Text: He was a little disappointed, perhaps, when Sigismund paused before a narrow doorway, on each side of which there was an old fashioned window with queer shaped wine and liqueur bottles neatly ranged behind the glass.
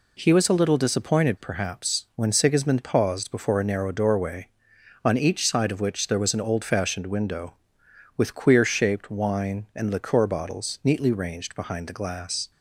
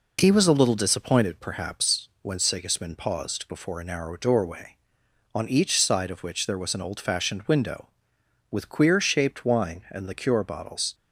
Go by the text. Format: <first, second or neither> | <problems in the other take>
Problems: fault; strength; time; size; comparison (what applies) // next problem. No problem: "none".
first | stops before "neatly ranged behind the glass"; at 10.9 s